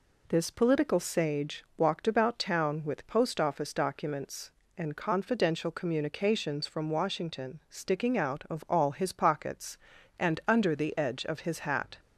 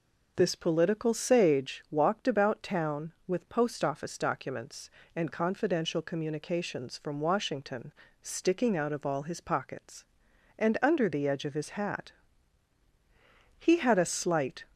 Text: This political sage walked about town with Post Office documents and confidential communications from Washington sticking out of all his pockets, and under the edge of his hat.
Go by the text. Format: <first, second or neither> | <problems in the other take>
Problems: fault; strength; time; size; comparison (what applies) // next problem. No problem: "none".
first | pauses between "Washington" and "sticking"; slight; at 7.9 s; 0.28 s long // goes on to say "He had a slight"; noticeable; from 13.5 s on; 1.0 s long